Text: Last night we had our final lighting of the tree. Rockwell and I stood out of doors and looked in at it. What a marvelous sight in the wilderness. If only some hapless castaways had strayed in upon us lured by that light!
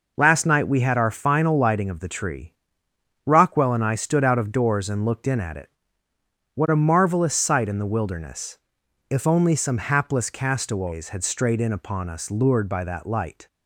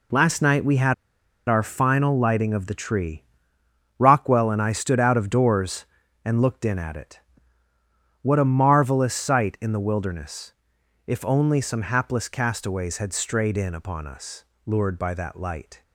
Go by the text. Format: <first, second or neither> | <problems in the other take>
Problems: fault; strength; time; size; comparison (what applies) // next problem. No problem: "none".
first | pauses between "had" and "our"; noticeable; at 0.9 s; 0.55 s long // pauses between "us" and "lured"; slight; at 14.4 s; 0.20 s long